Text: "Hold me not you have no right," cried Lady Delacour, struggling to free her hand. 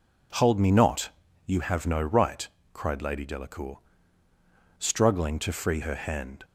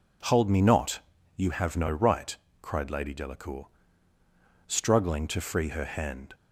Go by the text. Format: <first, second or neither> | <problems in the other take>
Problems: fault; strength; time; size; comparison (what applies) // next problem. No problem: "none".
neither | pauses between "not" and "you"; slight; the same in both